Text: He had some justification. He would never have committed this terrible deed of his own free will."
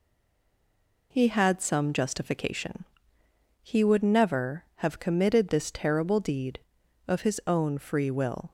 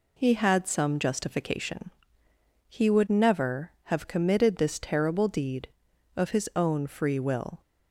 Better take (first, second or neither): second